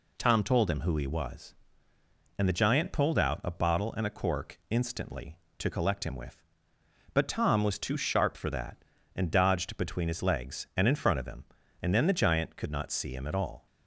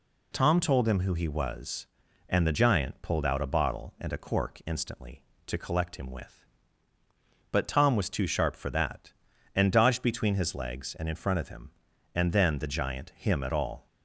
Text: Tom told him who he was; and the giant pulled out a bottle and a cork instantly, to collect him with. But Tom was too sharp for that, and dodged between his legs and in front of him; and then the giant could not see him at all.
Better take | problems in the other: first | skips "could not see"; at 13.1 s

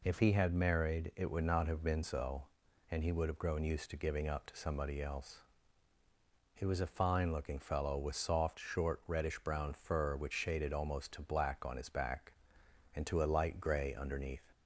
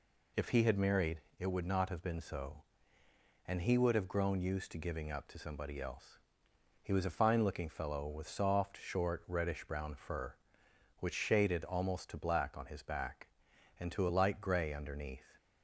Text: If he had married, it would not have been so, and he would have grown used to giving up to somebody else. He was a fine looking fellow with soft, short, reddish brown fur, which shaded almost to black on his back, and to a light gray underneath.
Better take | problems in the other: neither | none

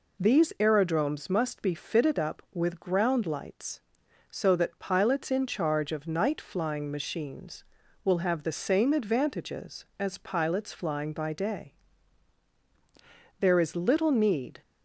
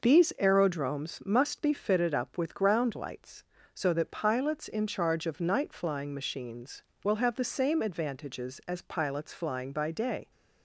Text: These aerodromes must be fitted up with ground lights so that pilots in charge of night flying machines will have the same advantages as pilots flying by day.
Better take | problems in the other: second | goes on to say "There is little need"; noticeable; from 13.3 s on; 1.2 s long

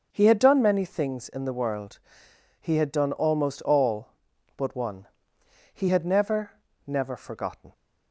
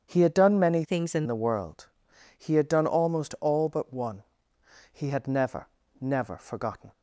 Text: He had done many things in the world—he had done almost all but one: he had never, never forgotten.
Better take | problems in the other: first | starts louder than the rest; strong; until 1.0 s; 8 dB // changes voice from "things" to "in"; from 0.8 to 1.2 s; 0.4 s long

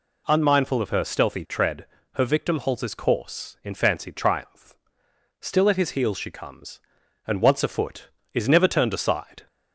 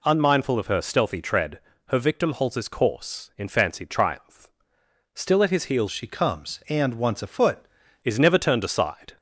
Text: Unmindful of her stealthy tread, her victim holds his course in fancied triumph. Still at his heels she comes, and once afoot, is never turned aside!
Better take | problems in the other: first | changes voice from "she" to "afoot"; from 5.9 to 7.6 s; 1.7 s long

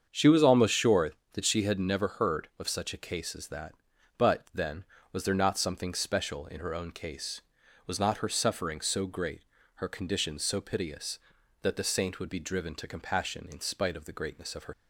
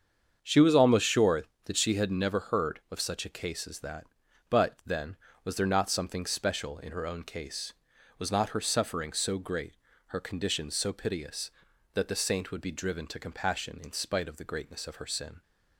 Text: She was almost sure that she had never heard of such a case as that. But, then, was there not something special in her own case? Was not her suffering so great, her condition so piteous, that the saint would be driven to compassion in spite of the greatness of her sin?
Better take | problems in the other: second | starts louder than the rest; strong; until 1.1 s; 7.5 dB; strong in the second // stops before "sin"; at 14.7 s

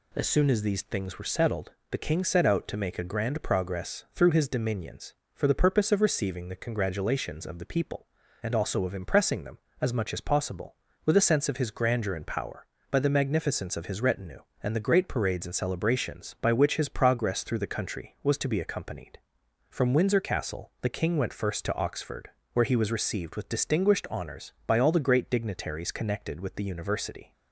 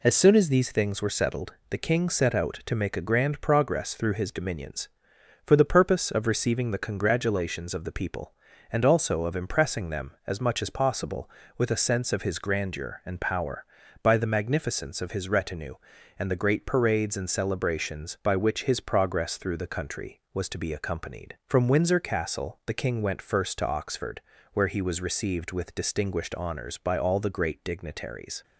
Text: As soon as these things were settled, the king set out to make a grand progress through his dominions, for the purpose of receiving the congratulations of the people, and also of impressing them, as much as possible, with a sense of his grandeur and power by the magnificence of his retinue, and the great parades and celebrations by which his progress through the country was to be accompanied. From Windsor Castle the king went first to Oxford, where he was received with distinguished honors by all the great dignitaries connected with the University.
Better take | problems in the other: first | stops before "connected with the University"; at 28.4 s

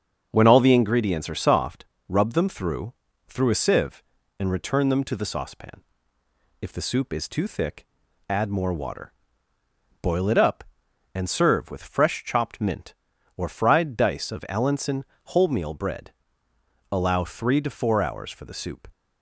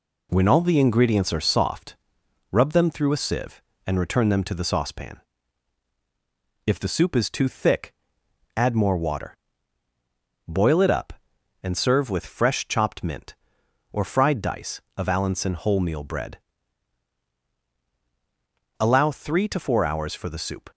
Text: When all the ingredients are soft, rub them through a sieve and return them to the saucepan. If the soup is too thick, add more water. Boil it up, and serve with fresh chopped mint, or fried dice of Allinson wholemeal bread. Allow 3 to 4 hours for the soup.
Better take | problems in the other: second | starts louder than the rest; strong; until 1.3 s; 7 dB // says "through" twice; at 3.2 s // pauses between "Allinson" and "wholemeal"; slight; at 15.0 s; 0.26 s long

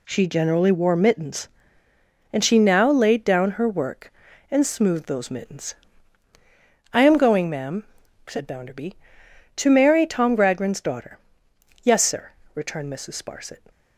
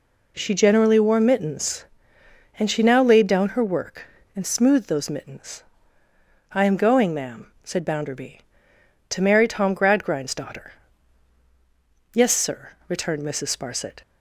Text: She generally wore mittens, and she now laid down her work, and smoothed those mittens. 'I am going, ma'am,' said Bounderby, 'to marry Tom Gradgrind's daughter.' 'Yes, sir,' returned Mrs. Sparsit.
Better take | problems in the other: neither | none

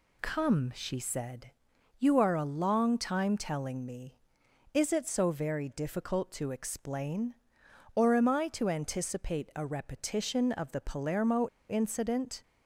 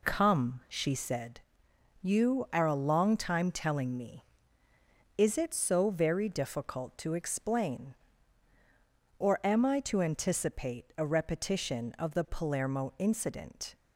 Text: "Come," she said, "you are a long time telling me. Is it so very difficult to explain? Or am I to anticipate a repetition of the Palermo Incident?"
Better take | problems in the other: second | pauses between "Palermo" and "Incident"; slight; at 11.4 s; 0.21 s long

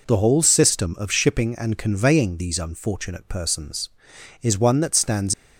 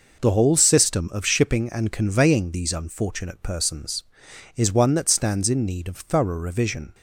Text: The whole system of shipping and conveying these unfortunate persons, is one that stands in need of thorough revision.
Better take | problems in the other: second | stops before "in need of thorough revision"; at 5.3 s

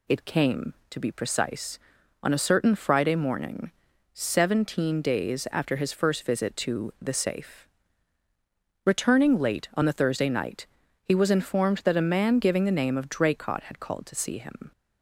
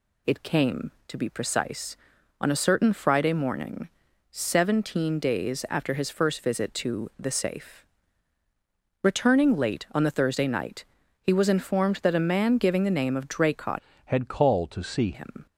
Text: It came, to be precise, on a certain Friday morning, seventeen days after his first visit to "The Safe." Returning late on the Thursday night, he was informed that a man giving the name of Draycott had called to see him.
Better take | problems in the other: first | changes voice from "had" to "see"; from 14.0 to 15.0 s; 1.0 s long

